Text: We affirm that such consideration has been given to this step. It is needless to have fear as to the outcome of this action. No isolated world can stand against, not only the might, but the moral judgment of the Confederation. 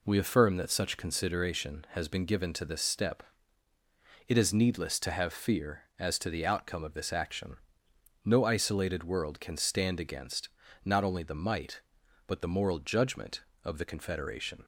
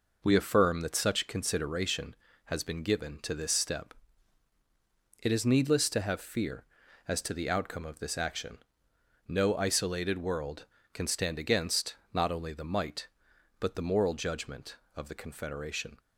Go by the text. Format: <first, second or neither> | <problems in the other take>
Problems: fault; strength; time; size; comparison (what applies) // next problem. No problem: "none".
neither | none